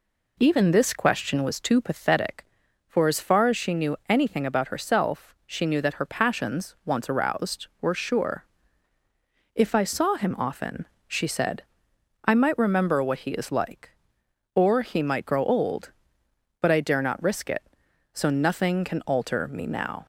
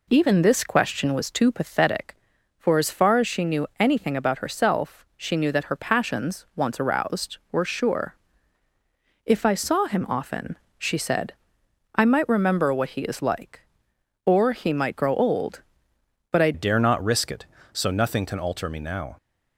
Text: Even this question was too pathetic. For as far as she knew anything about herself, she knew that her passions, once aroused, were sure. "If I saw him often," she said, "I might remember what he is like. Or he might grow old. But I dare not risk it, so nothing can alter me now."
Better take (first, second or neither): first